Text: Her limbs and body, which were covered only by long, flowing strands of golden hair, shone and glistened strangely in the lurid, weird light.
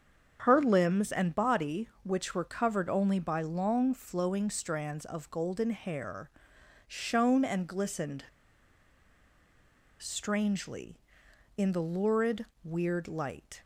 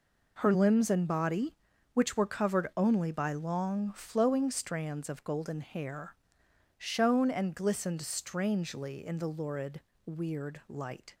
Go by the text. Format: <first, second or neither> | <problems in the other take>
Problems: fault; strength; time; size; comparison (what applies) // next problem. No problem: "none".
second | starts louder than the rest; strong; until 1.4 s; 7.5 dB // pauses between "glistened" and "strangely"; strong; at 8.2 s; 1.7 s long